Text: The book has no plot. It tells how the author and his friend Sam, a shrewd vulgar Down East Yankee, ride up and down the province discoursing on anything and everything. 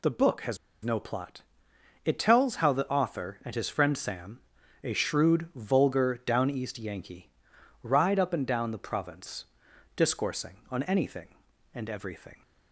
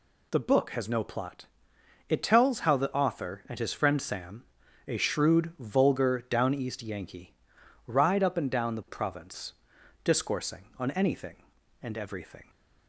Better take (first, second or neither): second